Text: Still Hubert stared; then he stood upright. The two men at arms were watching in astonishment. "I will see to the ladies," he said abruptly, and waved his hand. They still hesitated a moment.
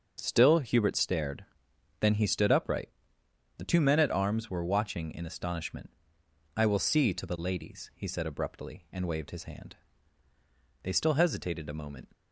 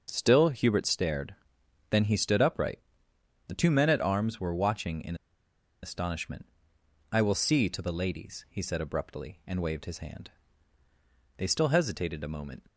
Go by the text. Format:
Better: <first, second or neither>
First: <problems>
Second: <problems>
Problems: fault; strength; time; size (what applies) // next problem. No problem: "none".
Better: first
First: none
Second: pauses between "in" and "astonishment"; noticeable; at 5.1 s; 0.67 s long